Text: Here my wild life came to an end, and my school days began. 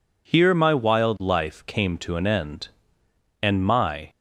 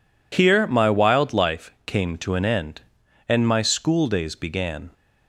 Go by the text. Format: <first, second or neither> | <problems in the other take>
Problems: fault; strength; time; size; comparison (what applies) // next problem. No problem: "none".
second | stops before "school days began"; at 4.0 s